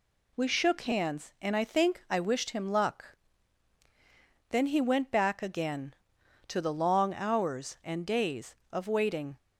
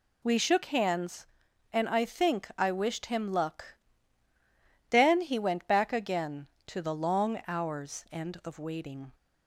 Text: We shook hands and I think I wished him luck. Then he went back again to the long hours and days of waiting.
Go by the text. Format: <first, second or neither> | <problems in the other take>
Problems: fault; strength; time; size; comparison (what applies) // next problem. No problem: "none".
first | skips "days"; at 8.4 s